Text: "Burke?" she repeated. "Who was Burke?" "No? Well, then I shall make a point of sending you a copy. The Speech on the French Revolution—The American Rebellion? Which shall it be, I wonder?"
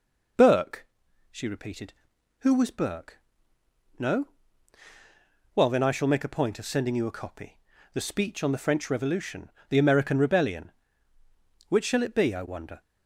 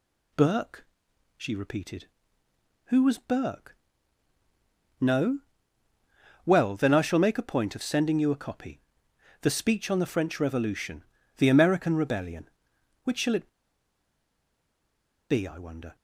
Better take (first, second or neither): first